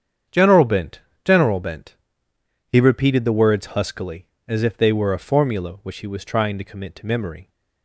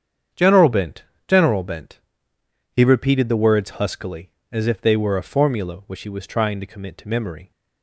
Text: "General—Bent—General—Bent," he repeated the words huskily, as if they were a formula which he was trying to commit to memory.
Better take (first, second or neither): neither